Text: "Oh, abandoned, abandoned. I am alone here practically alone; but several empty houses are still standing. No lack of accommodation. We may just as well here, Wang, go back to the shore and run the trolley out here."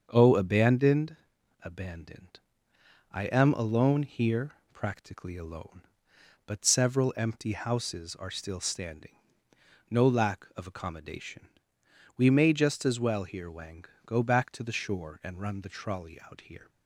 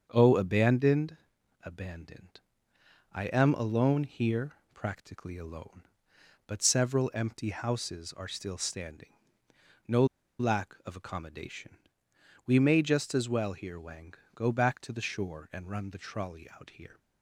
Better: first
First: starts louder than the rest; until 1.1 s; 7 dB // pauses between "here" and "practically"; slight; at 4.5 s; 0.20 s long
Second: starts louder than the rest; until 1.1 s; 7 dB // pauses between "here" and "practically"; slight; at 4.5 s; 0.20 s long // pauses between "No" and "lack"; slight; at 10.0 s; 0.34 s long

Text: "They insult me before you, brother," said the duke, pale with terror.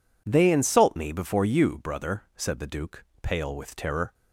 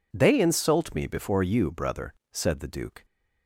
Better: first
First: none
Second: stops before "pale with terror"; at 3.0 s

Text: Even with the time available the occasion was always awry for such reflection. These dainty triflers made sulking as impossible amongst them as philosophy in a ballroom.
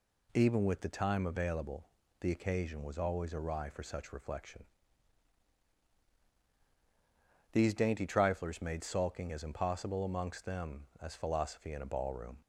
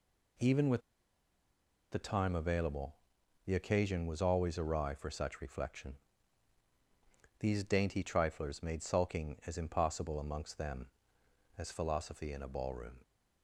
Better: first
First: pauses between "available" and "the"; slight; at 1.8 s; 0.32 s long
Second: pauses between "with" and "the"; at 0.8 s; 1.1 s long // pauses between "available" and "the"; noticeable; at 2.9 s; 0.50 s long

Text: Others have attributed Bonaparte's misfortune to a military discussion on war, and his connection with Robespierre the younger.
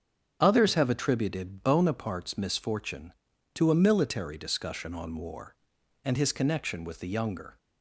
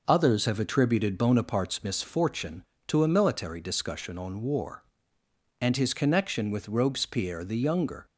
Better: second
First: starts louder than the rest; strong; until 1.4 s; 7 dB // skips "Robespierre"; at 6.9 s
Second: none

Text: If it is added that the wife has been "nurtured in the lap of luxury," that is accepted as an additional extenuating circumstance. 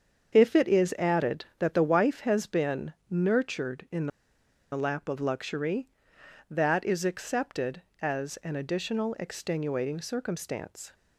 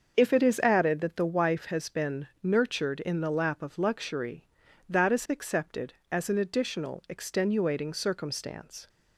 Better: second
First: starts louder than the rest; until 1.3 s; 7 dB // pauses between "in" and "the"; noticeable; at 4.0 s; 0.64 s long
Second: starts louder than the rest; until 1.1 s; 6.5 dB

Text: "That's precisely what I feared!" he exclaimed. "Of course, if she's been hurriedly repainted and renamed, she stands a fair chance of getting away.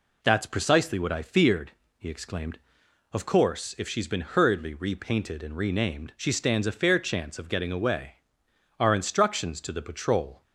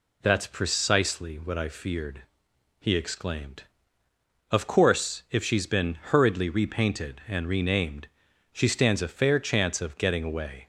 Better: second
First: goes on to say "Our instructions to the patrol"; from 8.8 s on; 1.6 s long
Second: none

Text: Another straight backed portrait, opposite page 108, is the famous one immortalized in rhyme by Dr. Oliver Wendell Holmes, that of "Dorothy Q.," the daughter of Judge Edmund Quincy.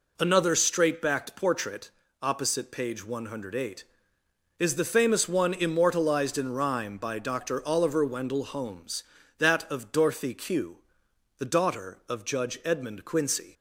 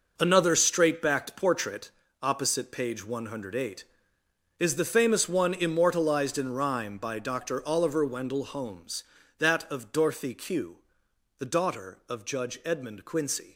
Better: first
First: none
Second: gets quieter; strong; throughout; 10 dB

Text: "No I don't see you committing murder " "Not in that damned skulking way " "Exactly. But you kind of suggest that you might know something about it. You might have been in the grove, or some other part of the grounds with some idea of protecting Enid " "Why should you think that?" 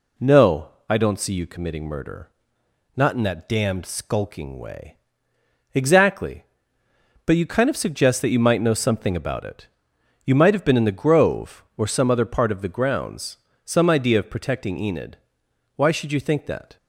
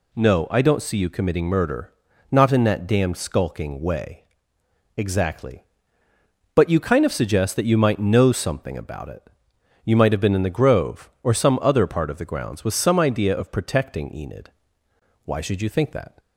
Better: second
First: pauses between "No" and "I"; slight; at 0.6 s; 0.20 s long // skips "with"; at 13.5 s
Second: none

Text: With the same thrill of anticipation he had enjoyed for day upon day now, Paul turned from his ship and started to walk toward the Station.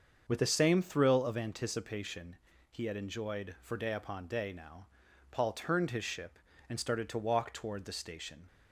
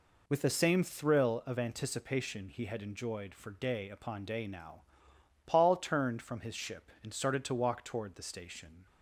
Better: second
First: starts louder than the rest; until 1.2 s; 7 dB // pauses between "anticipation" and "he"; slight; at 2.3 s; 0.34 s long // skips "from"; at 5.9 s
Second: none

